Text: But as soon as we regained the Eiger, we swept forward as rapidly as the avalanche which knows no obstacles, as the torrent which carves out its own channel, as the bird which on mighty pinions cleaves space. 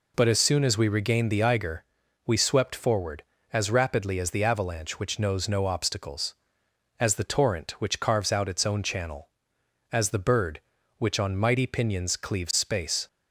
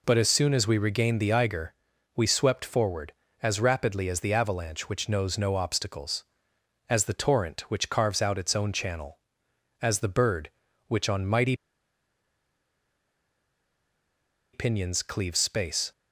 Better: first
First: none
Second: pauses between "mighty" and "pinions"; strong; at 11.5 s; 2.9 s long

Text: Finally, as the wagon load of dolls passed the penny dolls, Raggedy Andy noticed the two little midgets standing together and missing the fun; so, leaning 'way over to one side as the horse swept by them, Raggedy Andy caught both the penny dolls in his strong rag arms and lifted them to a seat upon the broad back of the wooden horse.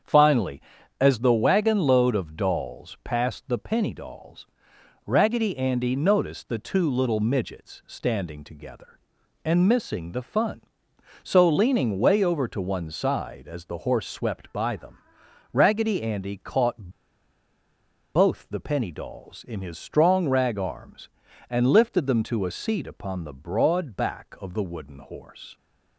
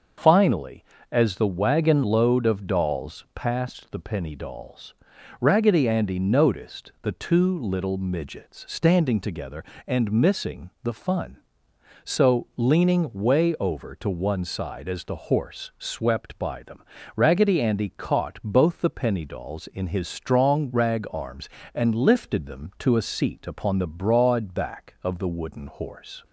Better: second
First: starts louder than the rest; strong; until 1.4 s; 7.5 dB // pauses between "caught" and "both"; strong; at 16.8 s; 1.2 s long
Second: starts louder than the rest; until 1.4 s; 6.5 dB

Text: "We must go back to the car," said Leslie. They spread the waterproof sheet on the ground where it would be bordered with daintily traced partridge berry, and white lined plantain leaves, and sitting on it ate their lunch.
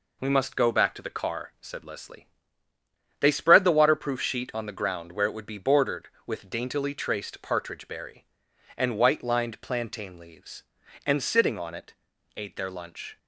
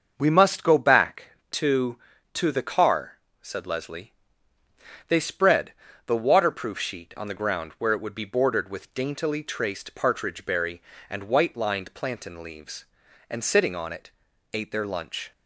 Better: first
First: pauses between "it" and "ate"; at 11.9 s; 0.42 s long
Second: starts louder than the rest; until 1.1 s; 6.5 dB // says "to" twice; at 2.3 s // pauses between "spread" and "the"; slight; at 5.7 s; 0.32 s long // pauses between "it" and "ate"; at 14.0 s; 0.44 s long

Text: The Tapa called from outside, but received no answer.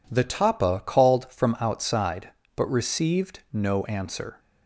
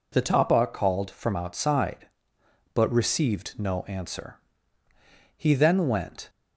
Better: first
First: none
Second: goes on to say "He then went"; noticeable; from 5.3 s on; 0.94 s long

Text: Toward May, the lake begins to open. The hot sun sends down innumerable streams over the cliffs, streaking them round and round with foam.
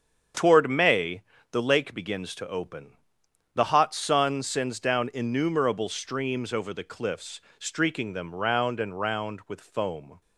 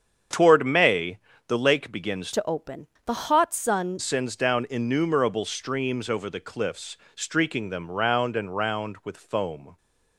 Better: first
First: starts louder than the rest; strong; until 1.6 s; 7.5 dB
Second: starts louder than the rest; strong; until 1.6 s; 7.5 dB // changes voice from "to" to "sun"; from 2.3 to 4.0 s; 1.7 s long

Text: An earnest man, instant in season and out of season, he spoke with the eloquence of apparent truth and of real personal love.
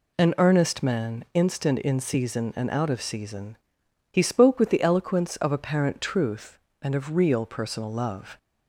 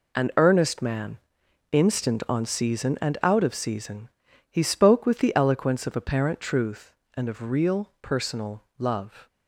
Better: first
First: none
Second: says "on" for "in"; at 2.2 s // pauses between "personal" and "love"; slight; at 8.6 s; 0.16 s long

